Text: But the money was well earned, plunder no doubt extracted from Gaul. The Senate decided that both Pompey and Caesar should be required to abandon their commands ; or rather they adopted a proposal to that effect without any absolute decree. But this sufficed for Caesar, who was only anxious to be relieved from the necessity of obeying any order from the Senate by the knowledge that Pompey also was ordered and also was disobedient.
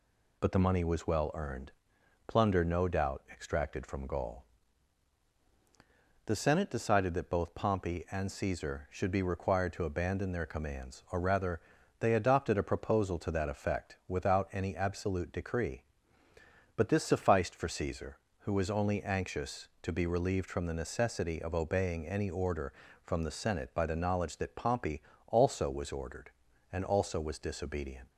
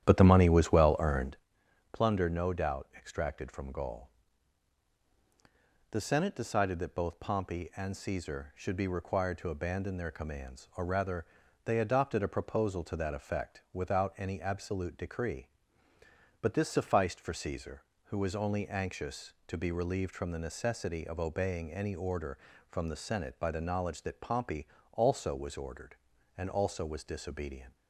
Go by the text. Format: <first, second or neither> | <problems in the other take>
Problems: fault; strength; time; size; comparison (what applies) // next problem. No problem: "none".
first | starts louder than the rest; strong; until 1.4 s; 11 dB // pauses between "rather" and "they"; at 11.2 s; 0.38 s long; also in the first // pauses between "Pompey" and "also"; slight; at 24.6 s; 0.26 s long; slight in the first